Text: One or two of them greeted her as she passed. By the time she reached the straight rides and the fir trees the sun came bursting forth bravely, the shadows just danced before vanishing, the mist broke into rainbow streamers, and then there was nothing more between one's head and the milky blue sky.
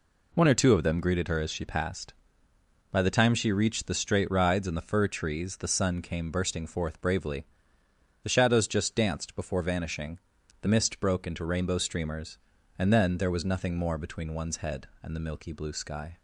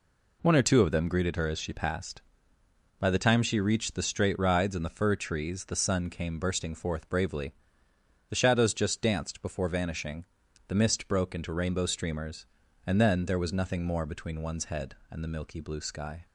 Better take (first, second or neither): neither